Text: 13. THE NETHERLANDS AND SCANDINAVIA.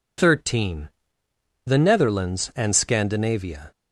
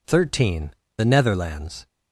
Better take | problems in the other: first | stops before "AND SCANDINAVIA"; at 1.8 s

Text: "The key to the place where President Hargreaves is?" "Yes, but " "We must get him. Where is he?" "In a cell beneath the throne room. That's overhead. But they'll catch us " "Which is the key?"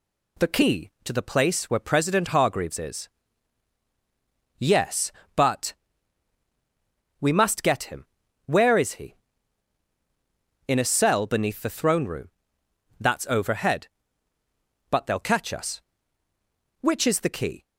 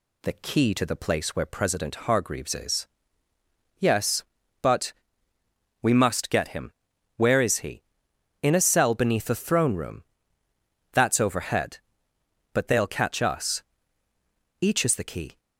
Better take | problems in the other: first | says "Each" for "Which"; at 14.6 s

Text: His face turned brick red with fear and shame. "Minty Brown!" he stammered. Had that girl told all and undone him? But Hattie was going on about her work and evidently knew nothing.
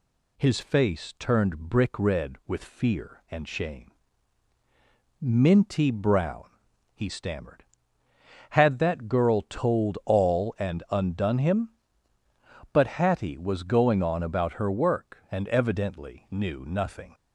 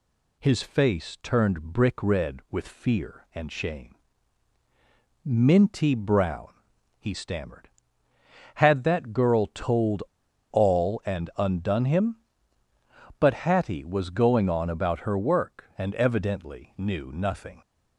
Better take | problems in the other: first | pauses between "told" and "all"; noticeable; at 10.0 s; 0.49 s long

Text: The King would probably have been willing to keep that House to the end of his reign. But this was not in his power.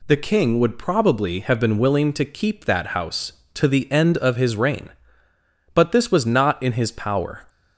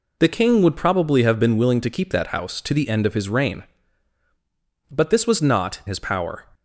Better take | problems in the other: first | skips "in"; at 5.8 s

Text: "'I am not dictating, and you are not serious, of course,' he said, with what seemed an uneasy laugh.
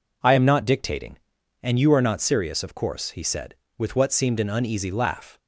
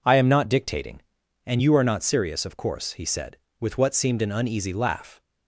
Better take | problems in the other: neither | none

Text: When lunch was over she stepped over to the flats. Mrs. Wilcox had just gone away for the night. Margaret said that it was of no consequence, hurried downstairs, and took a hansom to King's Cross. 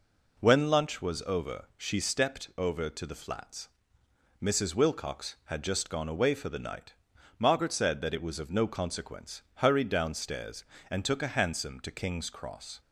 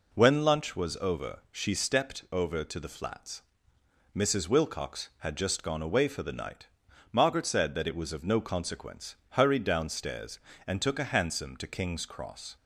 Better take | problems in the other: neither | none

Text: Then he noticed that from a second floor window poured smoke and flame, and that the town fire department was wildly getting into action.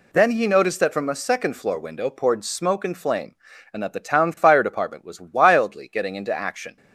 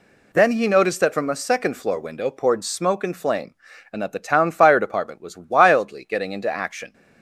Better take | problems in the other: neither | none

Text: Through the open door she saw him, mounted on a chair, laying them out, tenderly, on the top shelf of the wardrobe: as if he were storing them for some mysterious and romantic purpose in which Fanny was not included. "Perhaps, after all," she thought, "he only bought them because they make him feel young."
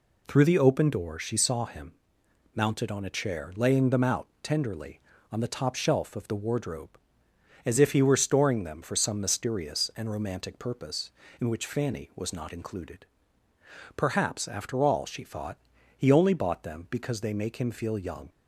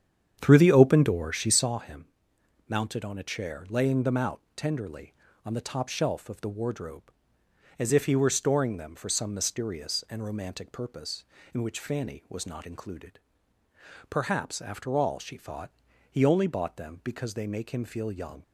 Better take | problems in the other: first | starts louder than the rest; strong; until 1.8 s; 8.5 dB

